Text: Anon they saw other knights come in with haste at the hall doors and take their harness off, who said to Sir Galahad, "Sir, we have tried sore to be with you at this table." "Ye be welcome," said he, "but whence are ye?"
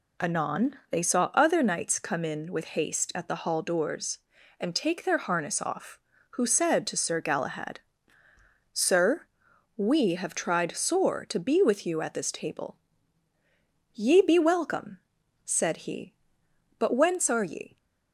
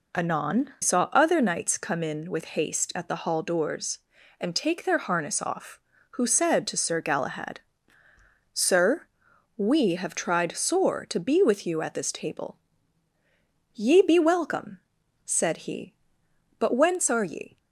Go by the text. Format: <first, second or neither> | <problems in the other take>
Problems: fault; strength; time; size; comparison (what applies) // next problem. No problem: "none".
first | skips "they"; at 0.7 s